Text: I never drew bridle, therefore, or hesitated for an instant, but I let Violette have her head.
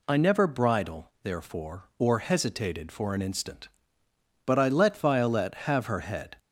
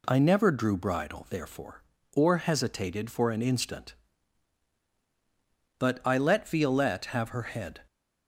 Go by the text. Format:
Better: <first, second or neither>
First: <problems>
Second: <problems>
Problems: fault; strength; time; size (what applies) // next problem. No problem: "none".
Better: second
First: skips "drew"; at 0.4 s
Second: none